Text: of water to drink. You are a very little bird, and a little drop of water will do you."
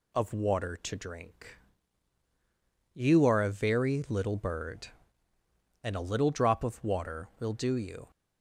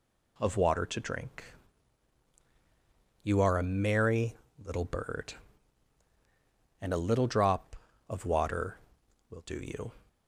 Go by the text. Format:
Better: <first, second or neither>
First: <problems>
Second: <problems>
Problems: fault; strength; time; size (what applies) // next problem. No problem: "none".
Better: first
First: none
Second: says "merry" for "very"; at 3.6 s